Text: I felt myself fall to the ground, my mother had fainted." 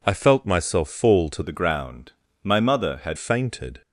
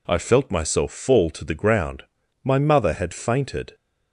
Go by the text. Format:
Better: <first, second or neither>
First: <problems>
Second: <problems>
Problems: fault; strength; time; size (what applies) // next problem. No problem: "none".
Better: second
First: changes voice from "the" to "had"; from 1.4 to 3.1 s; 1.7 s long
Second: none